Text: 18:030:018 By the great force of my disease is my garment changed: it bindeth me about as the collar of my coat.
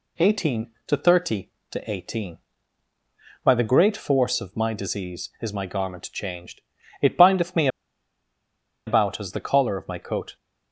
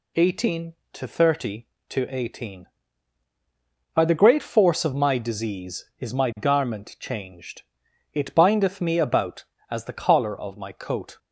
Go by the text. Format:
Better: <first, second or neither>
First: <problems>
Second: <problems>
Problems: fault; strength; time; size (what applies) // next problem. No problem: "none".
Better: second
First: pauses between "me" and "about"; at 7.6 s; 1.1 s long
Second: none